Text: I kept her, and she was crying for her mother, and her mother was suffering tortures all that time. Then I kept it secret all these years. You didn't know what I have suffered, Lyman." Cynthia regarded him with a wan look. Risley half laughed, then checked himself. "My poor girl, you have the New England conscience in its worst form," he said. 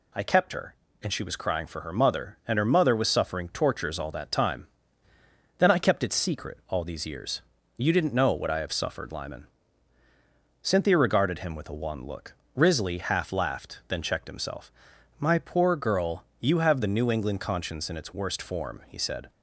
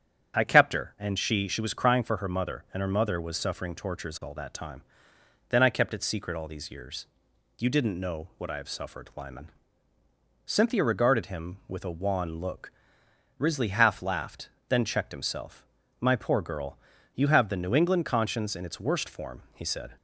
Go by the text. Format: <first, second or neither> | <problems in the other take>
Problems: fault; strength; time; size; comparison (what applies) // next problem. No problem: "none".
first | starts louder than the rest; strong; until 1.4 s; 8 dB // says "she" twice; at 1.4 s